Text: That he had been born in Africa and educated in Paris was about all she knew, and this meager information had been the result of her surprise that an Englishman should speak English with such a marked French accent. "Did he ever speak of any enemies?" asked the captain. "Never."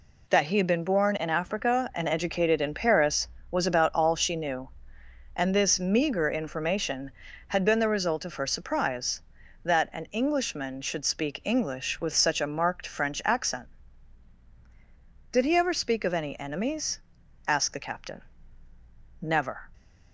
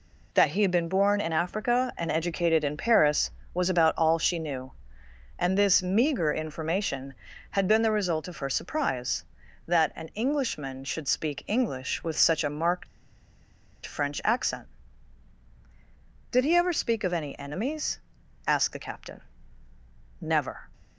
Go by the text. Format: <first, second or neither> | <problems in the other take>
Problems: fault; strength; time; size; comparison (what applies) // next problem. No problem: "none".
first | pauses between "marked" and "French"; at 12.8 s; 0.99 s long